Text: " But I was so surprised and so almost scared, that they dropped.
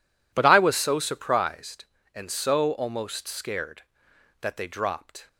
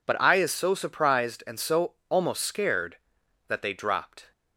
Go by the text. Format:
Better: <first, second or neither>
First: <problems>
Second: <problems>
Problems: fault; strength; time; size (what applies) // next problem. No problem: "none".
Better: first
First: none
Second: says "is" for "was"; at 0.3 s // pauses between "so" and "almost"; slight; at 1.9 s; 0.16 s long